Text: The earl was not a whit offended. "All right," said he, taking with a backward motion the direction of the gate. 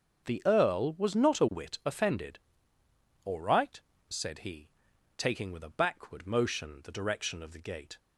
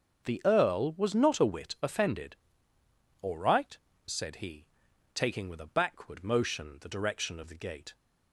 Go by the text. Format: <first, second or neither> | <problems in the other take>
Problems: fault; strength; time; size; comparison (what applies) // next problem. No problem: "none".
neither | starts louder than the rest; the same in both